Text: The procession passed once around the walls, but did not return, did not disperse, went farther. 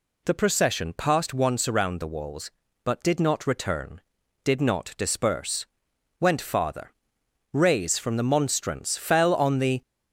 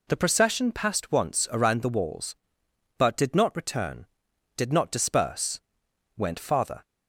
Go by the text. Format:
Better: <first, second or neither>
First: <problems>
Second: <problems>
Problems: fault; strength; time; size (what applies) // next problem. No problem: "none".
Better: second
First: goes on to say "Rays from the monstrance fell on the"; strong; from 7.5 s on; 2.2 s long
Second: none